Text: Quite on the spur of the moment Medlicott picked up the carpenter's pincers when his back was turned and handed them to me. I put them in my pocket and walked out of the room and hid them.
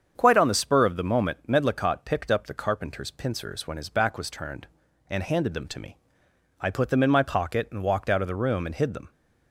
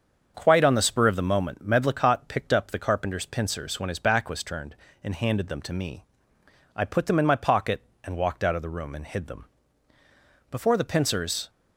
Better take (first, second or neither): first